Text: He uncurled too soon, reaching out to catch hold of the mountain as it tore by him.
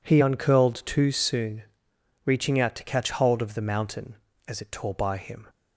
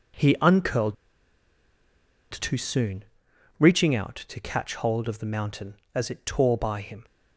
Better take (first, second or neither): first